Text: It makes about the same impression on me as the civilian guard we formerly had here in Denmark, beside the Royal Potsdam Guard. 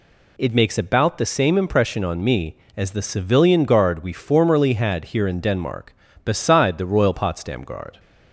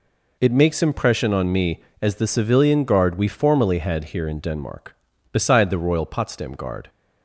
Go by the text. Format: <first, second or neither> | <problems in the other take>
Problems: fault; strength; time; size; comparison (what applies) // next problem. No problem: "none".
first | skips "about the same"; at 0.8 s